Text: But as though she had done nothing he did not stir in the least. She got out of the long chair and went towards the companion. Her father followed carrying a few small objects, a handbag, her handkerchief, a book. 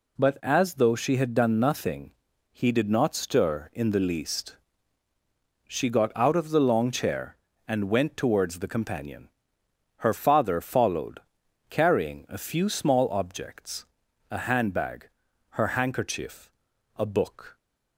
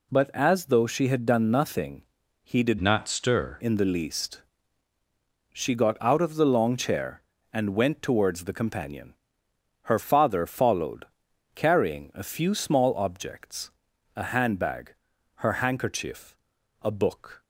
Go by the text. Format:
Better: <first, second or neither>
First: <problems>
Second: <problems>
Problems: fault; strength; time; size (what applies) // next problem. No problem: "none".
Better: first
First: pauses between "nothing" and "he"; at 2.1 s; 0.38 s long // pauses between "followed" and "carrying"; noticeable; at 11.2 s; 0.50 s long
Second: pauses between "nothing" and "he"; at 2.0 s; 0.38 s long // changes voice from "not" to "stir"; from 2.8 to 3.5 s; 0.7 s long // pauses between "followed" and "carrying"; noticeable; at 11.0 s; 0.50 s long